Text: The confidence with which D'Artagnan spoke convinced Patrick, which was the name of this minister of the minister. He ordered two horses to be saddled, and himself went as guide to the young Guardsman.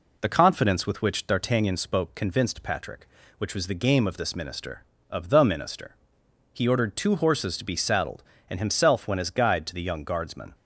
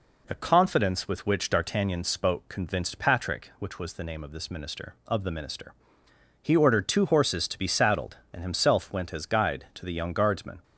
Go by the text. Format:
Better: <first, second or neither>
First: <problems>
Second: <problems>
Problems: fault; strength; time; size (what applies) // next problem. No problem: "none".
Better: second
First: says "game" for "name"; at 3.8 s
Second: none